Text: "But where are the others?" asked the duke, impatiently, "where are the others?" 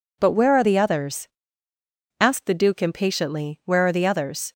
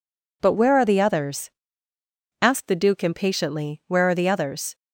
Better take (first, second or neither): neither